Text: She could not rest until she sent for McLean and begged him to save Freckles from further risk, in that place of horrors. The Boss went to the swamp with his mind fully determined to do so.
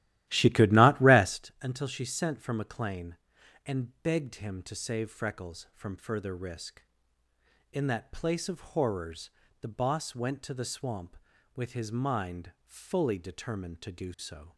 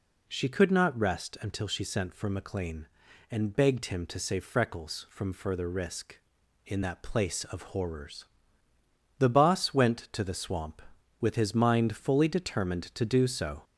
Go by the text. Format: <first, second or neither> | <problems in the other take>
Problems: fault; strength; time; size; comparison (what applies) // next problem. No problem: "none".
second | starts louder than the rest; strong; until 1.5 s; 14.5 dB